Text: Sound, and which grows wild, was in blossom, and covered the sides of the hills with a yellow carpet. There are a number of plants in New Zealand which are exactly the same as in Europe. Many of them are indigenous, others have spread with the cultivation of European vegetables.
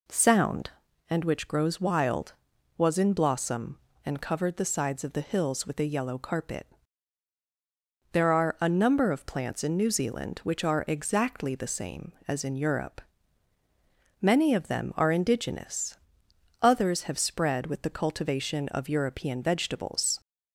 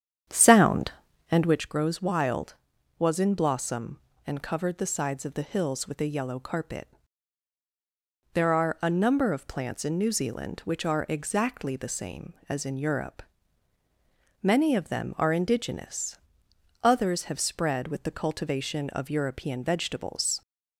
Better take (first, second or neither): first